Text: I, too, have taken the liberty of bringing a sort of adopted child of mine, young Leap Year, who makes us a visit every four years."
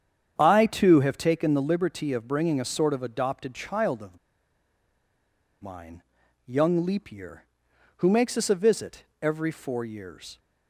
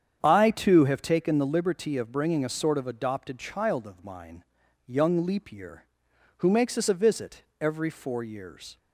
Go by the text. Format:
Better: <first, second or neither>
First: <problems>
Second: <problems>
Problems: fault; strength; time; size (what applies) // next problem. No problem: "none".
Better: second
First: starts louder than the rest; strong; until 1.3 s; 8.5 dB // pauses between "of" and "mine"; strong; at 4.1 s; 1.4 s long // pauses between "visit" and "every"; slight; at 9.0 s; 0.16 s long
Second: starts louder than the rest; strong; until 1.2 s; 8.5 dB // pauses between "visit" and "every"; slight; at 7.4 s; 0.16 s long